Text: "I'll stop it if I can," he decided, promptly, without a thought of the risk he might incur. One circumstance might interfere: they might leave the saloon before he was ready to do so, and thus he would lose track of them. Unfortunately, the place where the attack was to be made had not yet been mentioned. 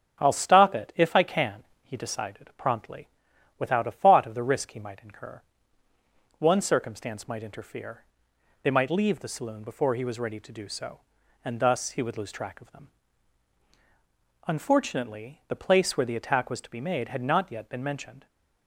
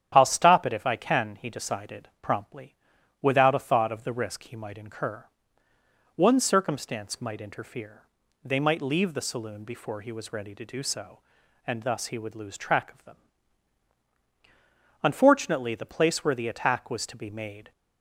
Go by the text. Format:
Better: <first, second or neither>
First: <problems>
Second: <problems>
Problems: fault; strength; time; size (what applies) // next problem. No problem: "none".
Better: first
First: starts louder than the rest; strong; until 1.2 s; 7.5 dB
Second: starts louder than the rest; strong; until 1.2 s; 10 dB // stops before "had not yet been mentioned"; at 17.7 s